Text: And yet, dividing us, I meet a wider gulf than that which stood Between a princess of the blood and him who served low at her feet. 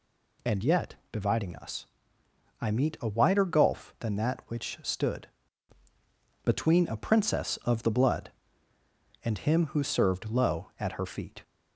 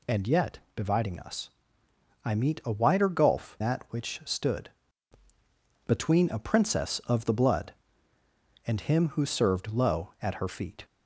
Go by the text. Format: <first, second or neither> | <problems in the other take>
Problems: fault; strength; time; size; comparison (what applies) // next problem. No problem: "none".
first | skips "than"; at 3.5 s // pauses between "stood" and "Between"; at 4.6 s; 1.1 s long; also in the first